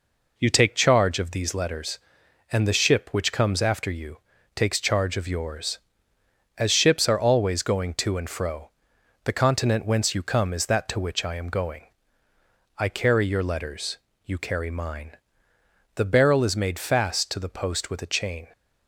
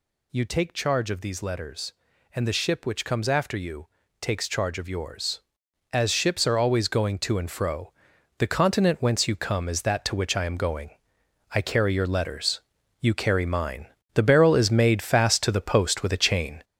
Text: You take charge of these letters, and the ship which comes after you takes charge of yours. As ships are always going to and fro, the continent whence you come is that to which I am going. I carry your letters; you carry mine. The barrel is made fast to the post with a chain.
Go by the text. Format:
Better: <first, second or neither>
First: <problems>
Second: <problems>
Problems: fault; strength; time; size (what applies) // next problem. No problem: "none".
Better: first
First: pauses between "you" and "takes"; slight; at 4.1 s; 0.36 s long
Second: gets louder; throughout; 6.5 dB // pauses between "you" and "takes"; slight; at 3.8 s; 0.32 s long